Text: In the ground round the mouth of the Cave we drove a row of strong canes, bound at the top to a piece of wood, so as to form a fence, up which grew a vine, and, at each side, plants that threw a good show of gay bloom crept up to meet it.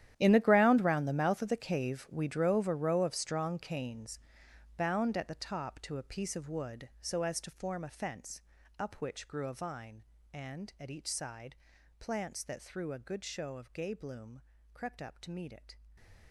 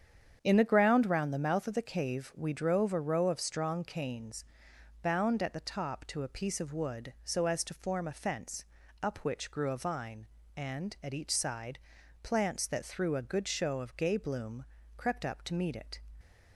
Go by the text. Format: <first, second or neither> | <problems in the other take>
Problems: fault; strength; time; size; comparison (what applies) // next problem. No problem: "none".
second | gets quieter; strong; throughout; 17.5 dB // starts louder than the rest; strong; until 1.1 s; 11.5 dB; strong in the second // pauses between "bloom" and "crept"; slight; at 14.4 s; 0.30 s long; slight in the second